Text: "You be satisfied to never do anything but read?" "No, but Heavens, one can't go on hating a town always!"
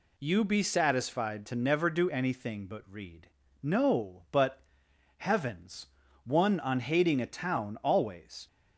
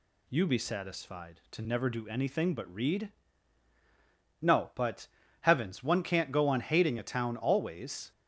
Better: second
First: pauses between "but" and "Heavens"; noticeable; at 4.6 s; 0.54 s long // skips "can't go"; at 6.6 s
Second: pauses between "but" and "Heavens"; slight; at 5.0 s; 0.36 s long

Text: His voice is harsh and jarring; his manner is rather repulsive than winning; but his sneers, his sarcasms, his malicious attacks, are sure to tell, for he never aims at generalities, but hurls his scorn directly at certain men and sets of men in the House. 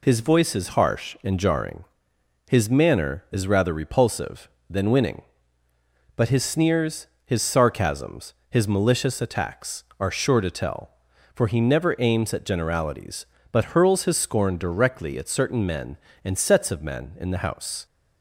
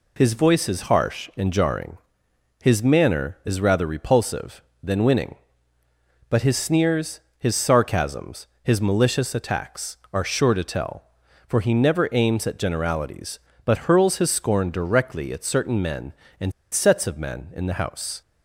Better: first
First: none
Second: pauses between "and" and "sets"; slight; at 16.5 s; 0.20 s long

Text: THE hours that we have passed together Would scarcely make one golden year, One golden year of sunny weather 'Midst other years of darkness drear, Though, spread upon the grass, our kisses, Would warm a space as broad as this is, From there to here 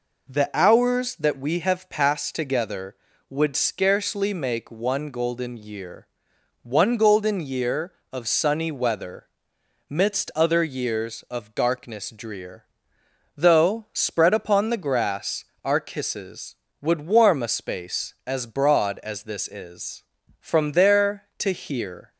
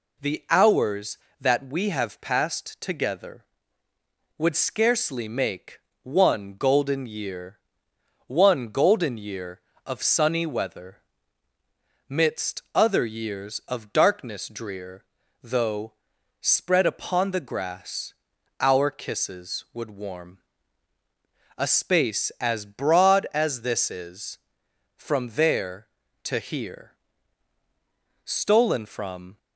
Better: first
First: pauses between "weather" and "Midst"; noticeable; at 9.2 s; 0.62 s long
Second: pauses between "make" and "one"; slight; at 5.7 s; 0.24 s long // pauses between "weather" and "Midst"; at 10.9 s; 1.1 s long // pauses between "warm" and "a"; at 20.3 s; 1.2 s long // goes on to say "Stolen from"; noticeable; from 28.2 s on; 1.1 s long

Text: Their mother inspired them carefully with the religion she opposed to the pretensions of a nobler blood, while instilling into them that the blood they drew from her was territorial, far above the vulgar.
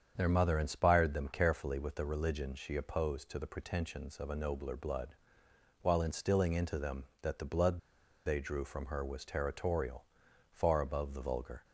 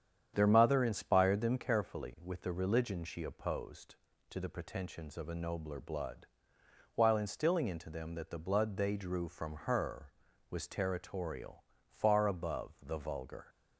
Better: second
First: starts louder than the rest; strong; until 1.1 s; 7.5 dB // pauses between "blood" and "they"; noticeable; at 7.7 s; 0.47 s long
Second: starts louder than the rest; strong; until 1.3 s; 8.5 dB

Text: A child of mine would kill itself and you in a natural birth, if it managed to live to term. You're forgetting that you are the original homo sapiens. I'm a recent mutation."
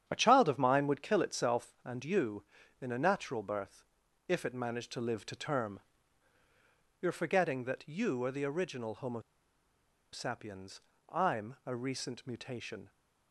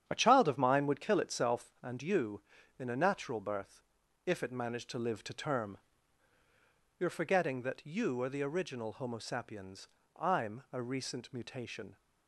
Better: second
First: starts louder than the rest; strong; until 1.0 s; 9 dB // pauses between "homo" and "sapiens"; noticeable; at 9.2 s; 0.92 s long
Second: starts louder than the rest; strong; until 1.0 s; 9 dB

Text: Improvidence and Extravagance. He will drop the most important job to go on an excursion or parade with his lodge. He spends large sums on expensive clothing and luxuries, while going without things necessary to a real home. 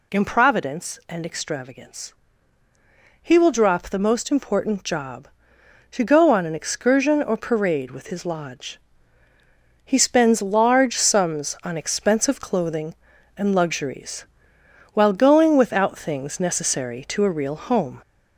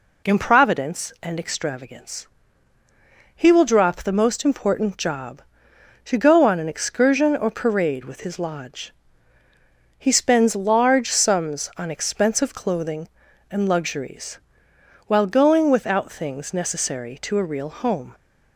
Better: second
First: gets louder; throughout; 3.5 dB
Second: none

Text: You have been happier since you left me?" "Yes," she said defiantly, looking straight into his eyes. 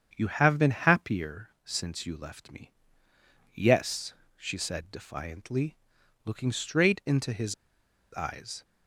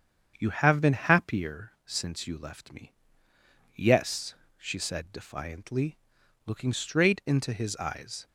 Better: second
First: starts louder than the rest; strong; until 1.1 s; 8 dB // pauses between "happier" and "since"; slight; at 1.4 s; 0.16 s long // pauses between "his" and "eyes"; noticeable; at 7.5 s; 0.58 s long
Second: starts louder than the rest; strong; until 1.3 s; 8 dB

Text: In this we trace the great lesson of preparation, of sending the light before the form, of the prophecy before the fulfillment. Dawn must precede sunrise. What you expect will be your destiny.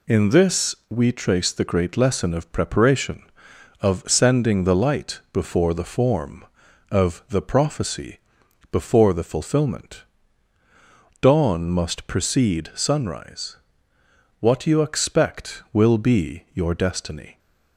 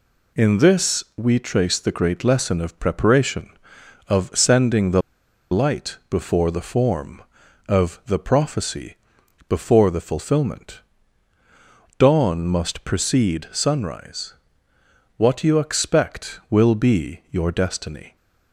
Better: first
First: pauses between "prophecy" and "before"; noticeable; at 8.1 s; 0.52 s long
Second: pauses between "the" and "light"; noticeable; at 5.0 s; 0.52 s long // pauses between "prophecy" and "before"; noticeable; at 8.9 s; 0.52 s long

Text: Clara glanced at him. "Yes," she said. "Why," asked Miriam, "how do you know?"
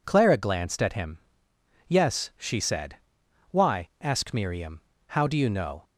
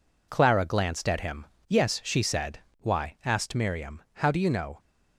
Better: neither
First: none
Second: none

